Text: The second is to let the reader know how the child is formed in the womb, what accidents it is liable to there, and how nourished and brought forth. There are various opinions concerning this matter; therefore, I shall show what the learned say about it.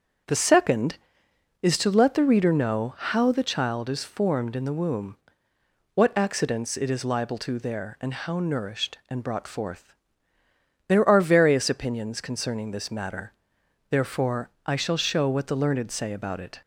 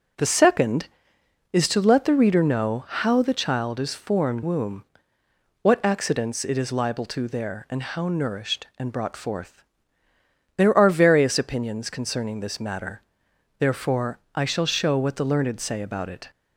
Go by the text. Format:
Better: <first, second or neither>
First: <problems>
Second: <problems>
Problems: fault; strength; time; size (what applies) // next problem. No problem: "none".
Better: first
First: starts louder than the rest; until 1.9 s; 7 dB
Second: starts louder than the rest; until 1.8 s; 6 dB // skips "in the"; at 4.4 s